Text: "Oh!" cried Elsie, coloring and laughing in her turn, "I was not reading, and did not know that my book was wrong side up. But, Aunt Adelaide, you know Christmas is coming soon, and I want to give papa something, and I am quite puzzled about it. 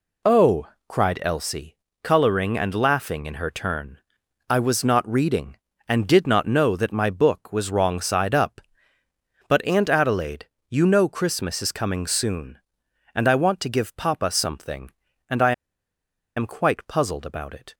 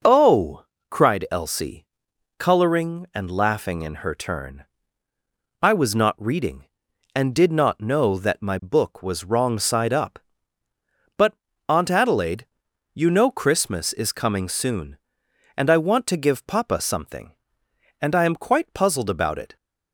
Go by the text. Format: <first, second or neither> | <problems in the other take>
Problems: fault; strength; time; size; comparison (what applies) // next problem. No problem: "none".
second | pauses between "I" and "am"; noticeable; at 15.5 s; 0.84 s long